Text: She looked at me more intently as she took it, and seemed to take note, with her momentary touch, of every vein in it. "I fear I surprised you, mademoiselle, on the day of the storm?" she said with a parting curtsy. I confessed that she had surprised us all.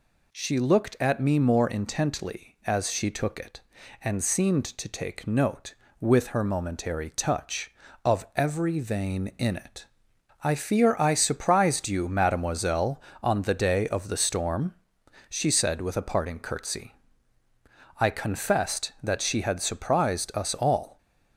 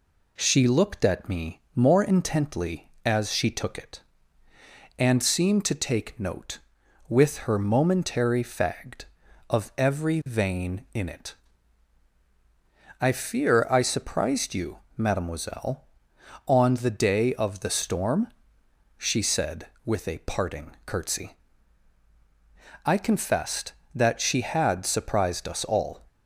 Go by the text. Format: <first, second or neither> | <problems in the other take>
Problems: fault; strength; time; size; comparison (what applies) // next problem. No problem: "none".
first | says "fagged" for "touch"; at 8.4 s